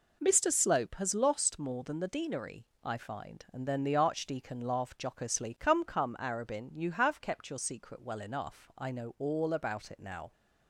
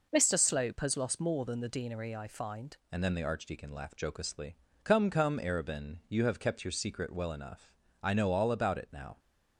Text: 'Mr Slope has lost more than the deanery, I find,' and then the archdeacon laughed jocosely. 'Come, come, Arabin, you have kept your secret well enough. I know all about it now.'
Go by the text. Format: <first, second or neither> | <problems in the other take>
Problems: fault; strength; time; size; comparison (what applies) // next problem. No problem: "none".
first | changes voice at "and"; from 2.9 s on; 6.2 s long